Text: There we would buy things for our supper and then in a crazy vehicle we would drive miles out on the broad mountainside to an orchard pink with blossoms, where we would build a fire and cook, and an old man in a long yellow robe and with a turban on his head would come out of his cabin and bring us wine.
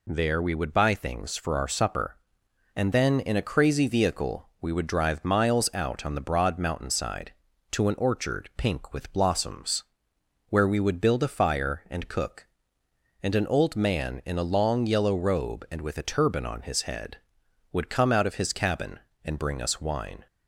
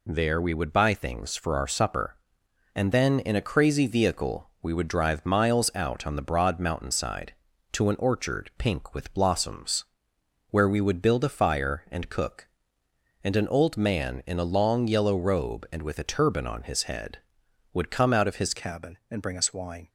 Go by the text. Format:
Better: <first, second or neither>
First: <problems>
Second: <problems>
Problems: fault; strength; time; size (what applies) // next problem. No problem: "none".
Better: first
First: none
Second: changes voice at "cabin"; from 18.5 s on; 1.3 s long